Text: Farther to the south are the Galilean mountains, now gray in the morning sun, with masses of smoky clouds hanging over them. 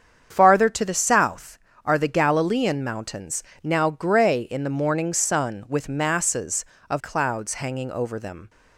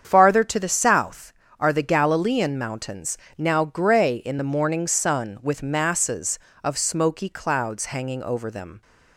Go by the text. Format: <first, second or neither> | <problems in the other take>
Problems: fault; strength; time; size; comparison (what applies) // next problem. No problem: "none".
second | starts louder than the rest; strong; until 1.3 s; 7.5 dB; strong in the second // skips "smoky"; at 6.9 s